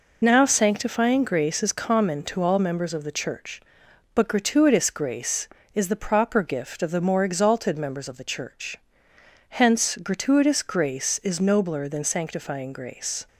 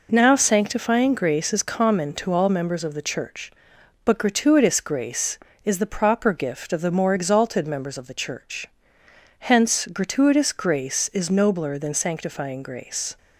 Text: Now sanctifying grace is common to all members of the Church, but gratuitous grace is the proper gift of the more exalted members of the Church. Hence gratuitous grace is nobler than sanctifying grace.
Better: second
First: loses the start of "Now"; at 0.2 s; 35 ms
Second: none

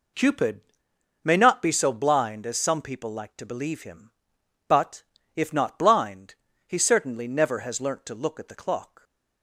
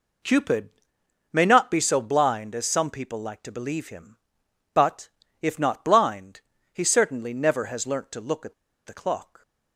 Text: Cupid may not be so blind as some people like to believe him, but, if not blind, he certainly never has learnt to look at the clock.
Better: first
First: pauses between "Cupid" and "may"; noticeable; at 0.6 s; 0.64 s long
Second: pauses between "Cupid" and "may"; noticeable; at 0.6 s; 0.64 s long // pauses between "at" and "the"; slight; at 8.5 s; 0.33 s long

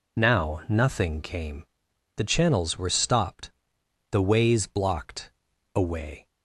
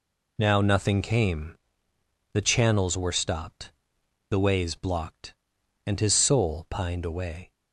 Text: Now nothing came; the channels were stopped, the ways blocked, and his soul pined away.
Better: second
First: skips "and his soul pined"; at 5.5 s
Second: none

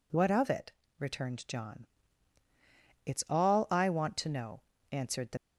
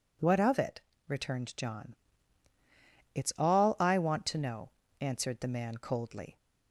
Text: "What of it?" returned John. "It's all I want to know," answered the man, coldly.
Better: second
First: stops before "man coldly"; at 5.3 s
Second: none

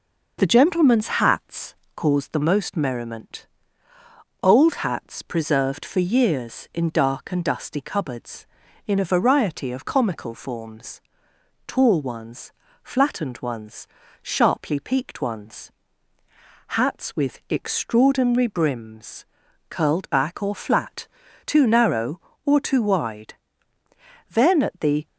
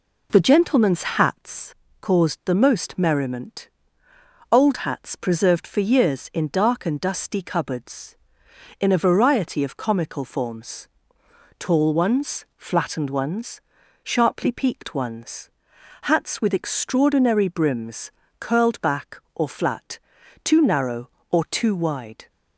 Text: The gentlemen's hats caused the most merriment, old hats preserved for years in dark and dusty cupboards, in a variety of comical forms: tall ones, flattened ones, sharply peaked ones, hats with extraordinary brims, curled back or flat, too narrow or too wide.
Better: second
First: pauses between "hats" and "caused"; slight; at 1.7 s; 0.20 s long // goes on to say "Then at the"; noticeable; from 24.2 s on; 0.78 s long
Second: pauses between "hats" and "caused"; slight; at 1.7 s; 0.24 s long

